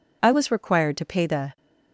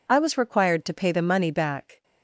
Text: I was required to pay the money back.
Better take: second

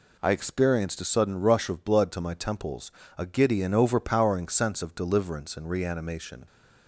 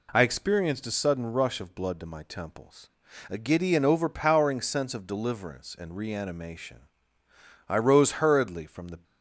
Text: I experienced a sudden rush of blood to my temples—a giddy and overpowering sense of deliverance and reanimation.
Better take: first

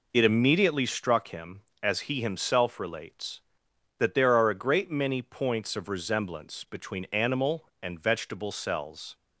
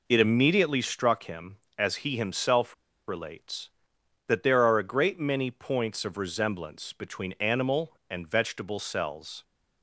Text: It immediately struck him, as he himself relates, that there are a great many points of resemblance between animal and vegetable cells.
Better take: first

